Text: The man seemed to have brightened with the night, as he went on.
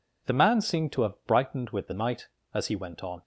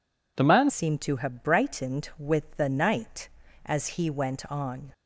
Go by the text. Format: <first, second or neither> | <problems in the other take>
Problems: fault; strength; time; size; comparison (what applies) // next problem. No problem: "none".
first | changes voice at "seemed"; from 0.6 s on; 4.3 s long